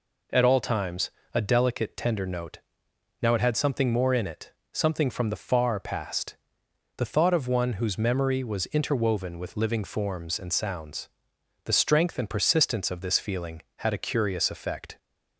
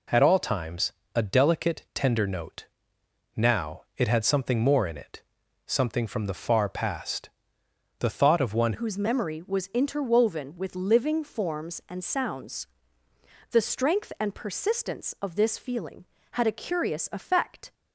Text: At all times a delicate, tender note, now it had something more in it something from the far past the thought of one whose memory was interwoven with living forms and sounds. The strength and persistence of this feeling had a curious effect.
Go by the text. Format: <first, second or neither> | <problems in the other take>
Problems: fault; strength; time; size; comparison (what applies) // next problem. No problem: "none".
first | pauses between "times" and "a"; slight; at 0.9 s; 0.22 s long; slight in the first // pauses between "it" and "something"; noticeable; at 5.2 s; 0.46 s long; slight in the first // pauses between "past" and "the"; noticeable; at 7.2 s; 0.70 s long; noticeable in the first // changes voice at "whose"; from 8.7 s on; 9.0 s long